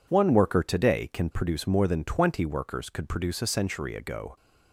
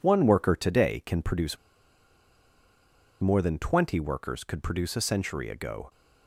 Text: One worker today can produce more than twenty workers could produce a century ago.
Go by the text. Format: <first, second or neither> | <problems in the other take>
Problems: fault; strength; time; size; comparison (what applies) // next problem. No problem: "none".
first | pauses between "produce" and "more"; strong; at 1.5 s; 1.6 s long